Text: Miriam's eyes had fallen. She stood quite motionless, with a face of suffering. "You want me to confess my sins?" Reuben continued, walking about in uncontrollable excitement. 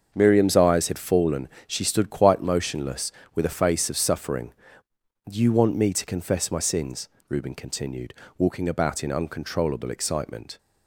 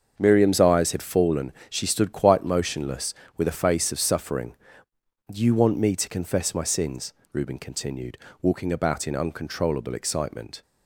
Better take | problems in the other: neither | starts louder than the rest; the same in both

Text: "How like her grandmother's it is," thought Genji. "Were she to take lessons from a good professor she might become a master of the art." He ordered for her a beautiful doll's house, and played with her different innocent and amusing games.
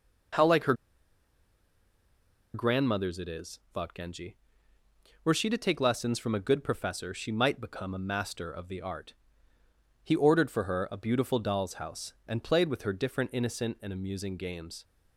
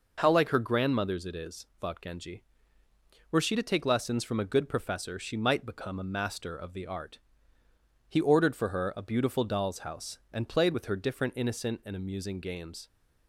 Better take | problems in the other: second | pauses between "her" and "grandmother's"; strong; at 0.7 s; 1.8 s long

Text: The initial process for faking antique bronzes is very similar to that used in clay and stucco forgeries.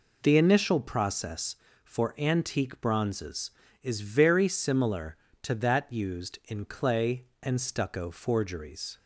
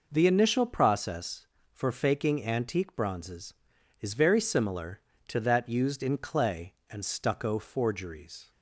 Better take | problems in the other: second | skips "faking"; at 2.1 s

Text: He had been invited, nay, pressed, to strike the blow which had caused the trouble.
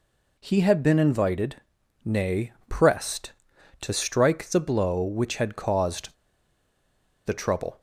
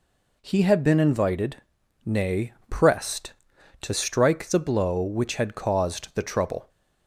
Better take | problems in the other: second | pauses between "caused" and "the"; at 6.1 s; 1.1 s long

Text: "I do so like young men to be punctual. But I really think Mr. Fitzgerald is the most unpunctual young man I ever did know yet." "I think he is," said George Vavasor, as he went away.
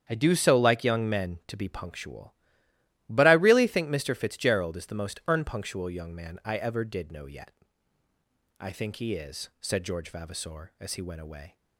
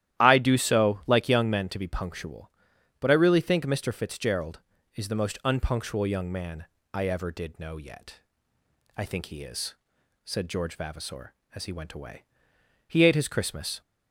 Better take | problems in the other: first | starts louder than the rest; strong; until 1.2 s; 12.5 dB; strong in the first // pauses between "man" and "I"; slight; at 6.6 s; 0.26 s long // goes on to say "He ate his Christmas"; noticeable; from 12.8 s on; 0.94 s long

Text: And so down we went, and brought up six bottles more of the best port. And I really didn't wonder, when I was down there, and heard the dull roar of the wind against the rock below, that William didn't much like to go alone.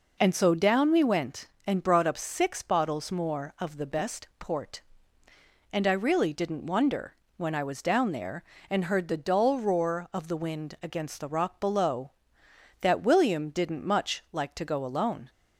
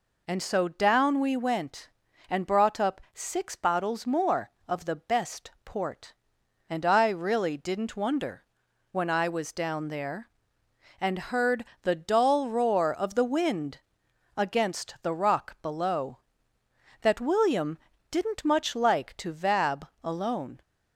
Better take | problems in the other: first | pauses between "heard" and "the"; slight; at 11.6 s; 0.16 s long // pauses between "wind" and "against"; noticeable; at 13.7 s; 0.58 s long // pauses between "William" and "didn't"; slight; at 17.7 s; 0.32 s long // says "vab" for "go"; at 19.3 s

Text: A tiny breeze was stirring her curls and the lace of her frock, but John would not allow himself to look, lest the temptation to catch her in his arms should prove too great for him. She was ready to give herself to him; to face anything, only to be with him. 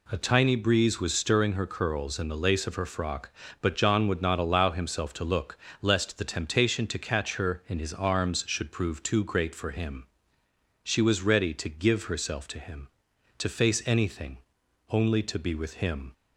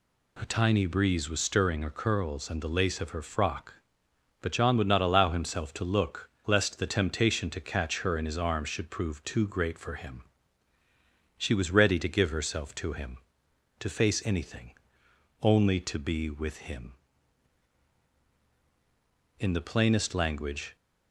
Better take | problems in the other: first | goes on to say "In the plainest language"; from 19.3 s on; 1.3 s long

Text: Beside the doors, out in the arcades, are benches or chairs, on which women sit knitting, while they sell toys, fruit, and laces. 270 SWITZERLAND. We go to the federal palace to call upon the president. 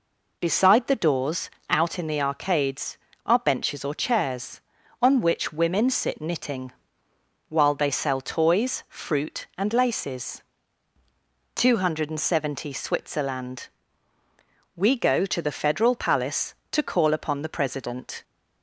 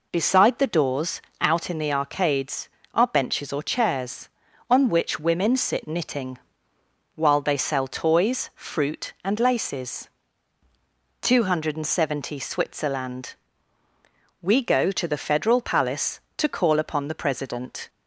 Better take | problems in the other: neither | none

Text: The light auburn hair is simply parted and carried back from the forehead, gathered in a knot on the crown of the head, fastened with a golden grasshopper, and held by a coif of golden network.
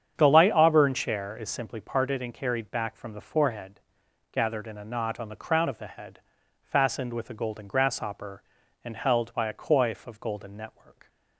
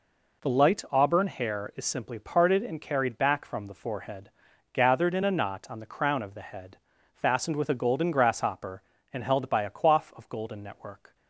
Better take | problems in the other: second | starts louder than the rest; strong; until 1.1 s; 8 dB // says "chair" for "hair"; at 0.9 s

